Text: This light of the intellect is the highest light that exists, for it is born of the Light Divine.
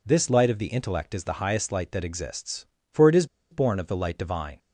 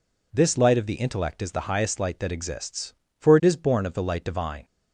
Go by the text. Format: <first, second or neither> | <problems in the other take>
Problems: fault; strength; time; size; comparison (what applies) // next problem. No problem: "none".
second | pauses between "is" and "born"; slight; at 3.2 s; 0.26 s long